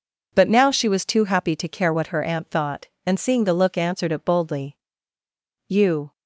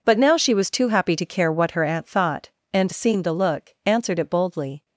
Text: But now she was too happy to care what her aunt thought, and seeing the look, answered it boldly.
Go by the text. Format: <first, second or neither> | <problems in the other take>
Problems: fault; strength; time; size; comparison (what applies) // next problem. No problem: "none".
second | goes on to say "You"; slight; from 5.6 s on; 0.44 s long